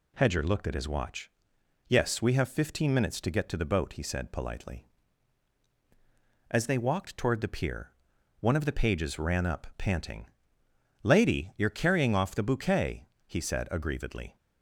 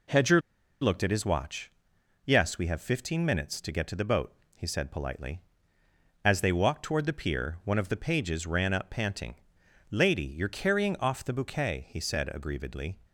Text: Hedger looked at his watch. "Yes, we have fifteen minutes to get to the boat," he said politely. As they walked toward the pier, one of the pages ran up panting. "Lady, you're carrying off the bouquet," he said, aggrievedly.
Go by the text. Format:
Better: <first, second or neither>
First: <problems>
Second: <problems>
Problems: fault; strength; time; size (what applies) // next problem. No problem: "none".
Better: first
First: none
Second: pauses between "Hedger" and "looked"; at 0.4 s; 0.40 s long